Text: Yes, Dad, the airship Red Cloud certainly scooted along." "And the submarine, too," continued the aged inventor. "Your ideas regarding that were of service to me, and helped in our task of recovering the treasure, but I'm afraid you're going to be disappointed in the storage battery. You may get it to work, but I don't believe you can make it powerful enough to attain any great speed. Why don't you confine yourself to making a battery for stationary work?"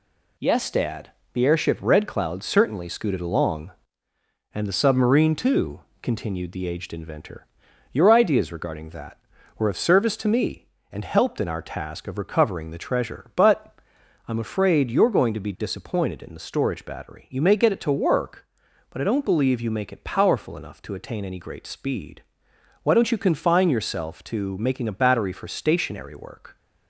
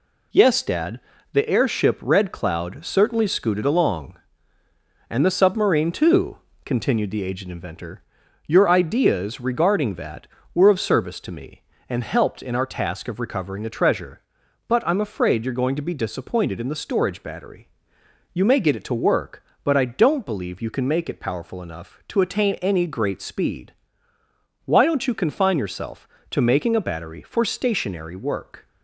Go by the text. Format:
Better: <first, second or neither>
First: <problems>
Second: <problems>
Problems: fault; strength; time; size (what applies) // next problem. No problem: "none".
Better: second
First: pauses between "but" and "I'm"; noticeable; at 13.7 s; 0.48 s long // skips "can"; at 19.7 s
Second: none